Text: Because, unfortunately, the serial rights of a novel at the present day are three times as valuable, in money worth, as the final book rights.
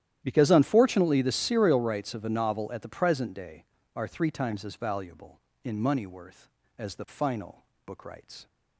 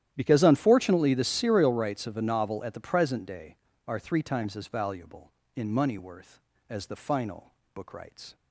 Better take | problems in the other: neither | starts louder than the rest; strong; the same in both // pauses between "final" and "book"; slight; the same in both

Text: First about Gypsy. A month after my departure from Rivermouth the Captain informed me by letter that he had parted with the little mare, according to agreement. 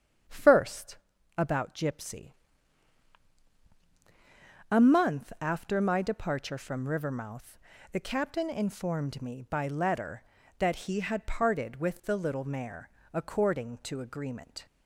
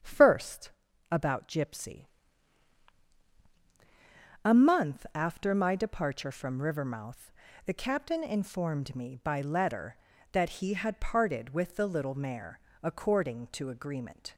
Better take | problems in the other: neither | starts louder than the rest; strong; the same in both // pauses between "First" and "about"; the same in both // pauses between "Rivermouth" and "the"; slight; the same in both

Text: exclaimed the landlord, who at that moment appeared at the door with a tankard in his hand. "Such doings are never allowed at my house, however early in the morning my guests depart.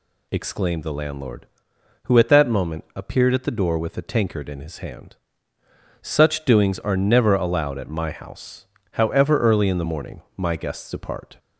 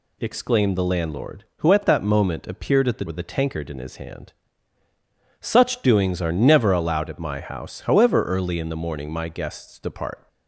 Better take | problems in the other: first | skips "door"; at 3.0 s

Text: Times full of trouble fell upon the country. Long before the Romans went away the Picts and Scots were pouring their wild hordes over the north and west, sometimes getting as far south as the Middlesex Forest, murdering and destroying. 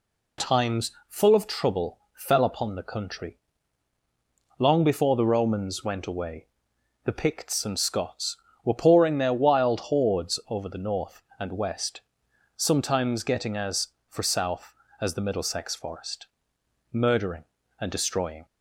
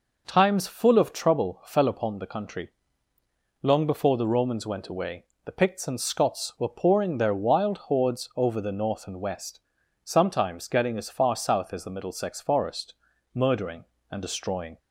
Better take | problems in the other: second | pauses between "Times" and "full"; slight; at 0.9 s; 0.18 s long // pauses between "trouble" and "fell"; slight; at 1.9 s; 0.16 s long // pauses between "away" and "the"; noticeable; at 6.4 s; 0.60 s long; slight in the second // says "for" for "far"; at 14.0 s

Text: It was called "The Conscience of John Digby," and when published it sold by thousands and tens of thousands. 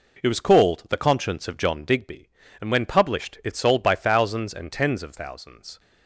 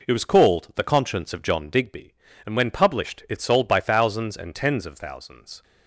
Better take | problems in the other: neither | none

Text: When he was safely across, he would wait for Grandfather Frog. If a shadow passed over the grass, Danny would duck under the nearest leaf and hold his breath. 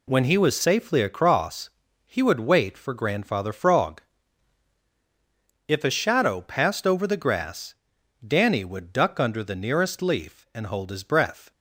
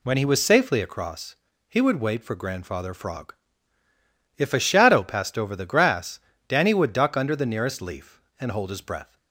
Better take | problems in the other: neither | none

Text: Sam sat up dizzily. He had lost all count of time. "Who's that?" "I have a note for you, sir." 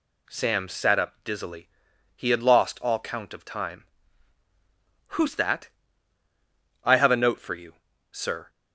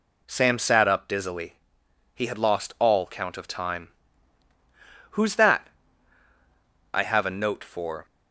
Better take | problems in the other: first | stops before "you sir"; at 8.0 s

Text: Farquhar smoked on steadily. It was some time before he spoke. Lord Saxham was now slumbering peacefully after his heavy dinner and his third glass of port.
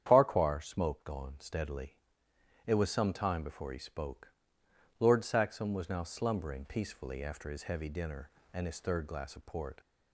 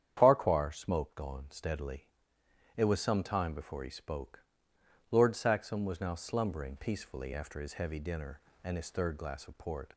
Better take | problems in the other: neither | starts louder than the rest; strong; the same in both

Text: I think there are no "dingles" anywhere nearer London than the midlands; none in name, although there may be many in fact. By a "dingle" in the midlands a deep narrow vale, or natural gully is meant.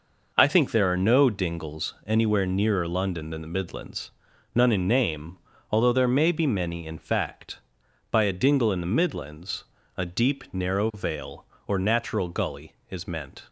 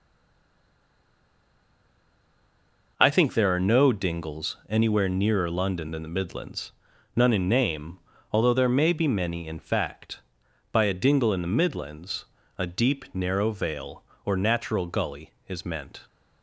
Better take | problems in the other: first | stays silent before the first word; strong; until 2.9 s; 2.9 s long // pauses between "midlands" and "a"; slight; at 12.2 s; 0.30 s long; slight in the first

